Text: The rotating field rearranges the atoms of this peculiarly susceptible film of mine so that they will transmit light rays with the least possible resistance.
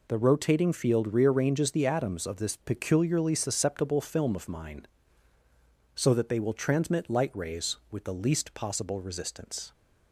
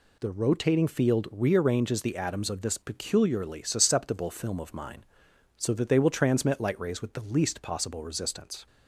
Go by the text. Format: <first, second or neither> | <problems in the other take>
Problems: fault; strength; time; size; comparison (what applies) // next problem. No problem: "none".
neither | none